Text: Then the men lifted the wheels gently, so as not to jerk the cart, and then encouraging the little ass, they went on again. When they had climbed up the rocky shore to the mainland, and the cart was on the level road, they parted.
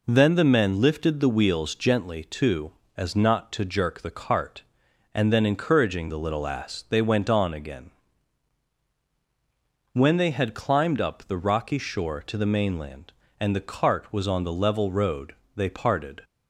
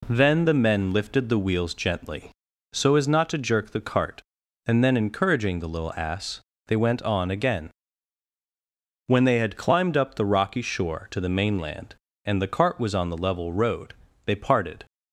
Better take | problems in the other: second | says "too" for "so"; at 2.2 s

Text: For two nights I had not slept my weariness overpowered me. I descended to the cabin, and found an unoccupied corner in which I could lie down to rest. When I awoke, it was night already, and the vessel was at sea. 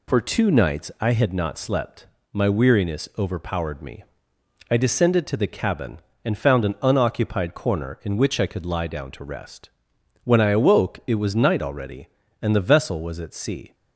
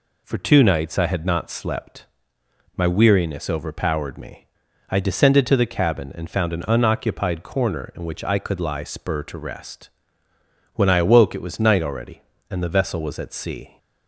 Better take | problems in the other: first | pauses between "slept" and "my"; noticeable; at 2.0 s; 0.70 s long; slight in the first // says "spur" for "down"; at 8.8 s

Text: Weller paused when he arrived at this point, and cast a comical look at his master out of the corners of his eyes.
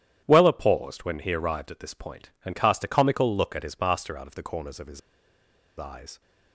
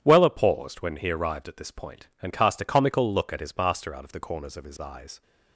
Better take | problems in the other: second | starts louder than the rest; strong; until 1.2 s; 10.5 dB; strong in the second // pauses between "his" and "eyes"; noticeable; at 5.0 s; 0.78 s long

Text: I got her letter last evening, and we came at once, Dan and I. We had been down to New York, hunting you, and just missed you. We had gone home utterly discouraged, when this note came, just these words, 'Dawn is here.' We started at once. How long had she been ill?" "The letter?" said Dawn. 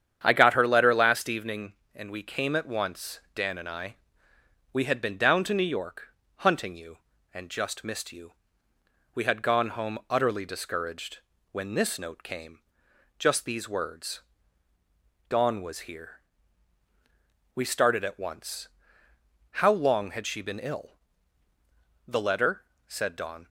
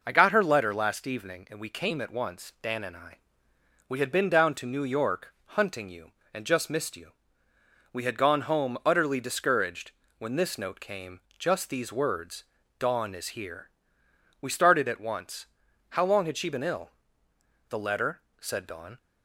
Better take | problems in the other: second | starts louder than the rest; strong; until 1.2 s; 8.5 dB // says "was" for "is"; at 15.5 s

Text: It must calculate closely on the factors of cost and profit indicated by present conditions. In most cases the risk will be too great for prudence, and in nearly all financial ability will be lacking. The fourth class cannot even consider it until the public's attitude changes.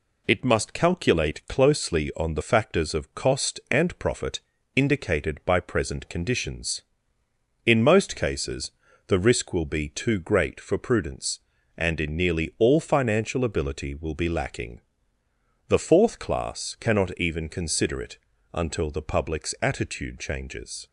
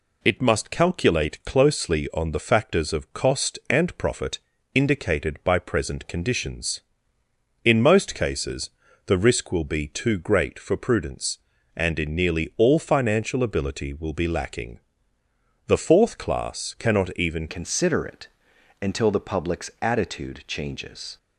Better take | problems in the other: first | pauses between "profit" and "indicated"; at 4.3 s; 0.38 s long; also in the first // pauses between "cases" and "the"; at 8.6 s; 0.38 s long; also in the first // changes voice at "consider"; from 17.4 s on; 3.7 s long // pauses between "it" and "until"; noticeable; at 18.2 s; 0.52 s long; slight in the first

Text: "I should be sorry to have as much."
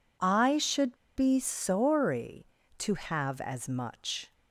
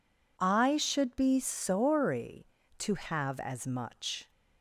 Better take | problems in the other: second | pauses between "should" and "be"; slight; at 0.9 s; 0.20 s long

